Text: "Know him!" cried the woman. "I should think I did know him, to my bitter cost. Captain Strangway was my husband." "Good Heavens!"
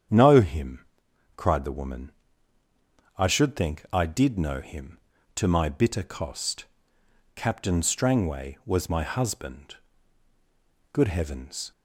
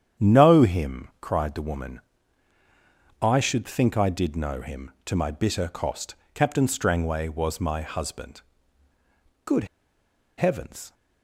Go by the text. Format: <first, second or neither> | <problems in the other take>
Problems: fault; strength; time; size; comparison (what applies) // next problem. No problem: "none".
first | starts louder than the rest; strong; until 1.3 s; 9 dB; strong in the first // pauses between "Good" and "Heavens"; noticeable; at 9.6 s; 0.72 s long